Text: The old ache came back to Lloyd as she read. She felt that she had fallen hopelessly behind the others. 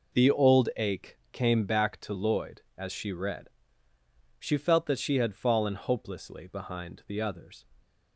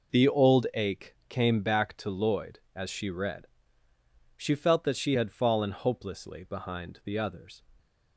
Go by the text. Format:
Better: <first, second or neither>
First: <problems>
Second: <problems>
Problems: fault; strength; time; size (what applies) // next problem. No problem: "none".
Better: neither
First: none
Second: none